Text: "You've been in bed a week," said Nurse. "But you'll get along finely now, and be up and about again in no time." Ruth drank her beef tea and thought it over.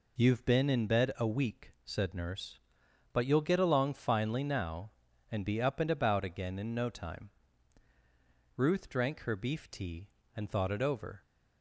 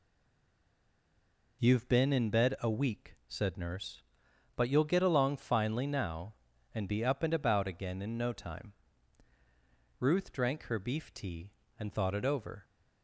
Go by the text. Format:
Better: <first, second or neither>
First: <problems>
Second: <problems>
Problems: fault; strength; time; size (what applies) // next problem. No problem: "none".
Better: first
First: none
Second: stays silent before the first word; noticeable; until 1.5 s; 1.5 s long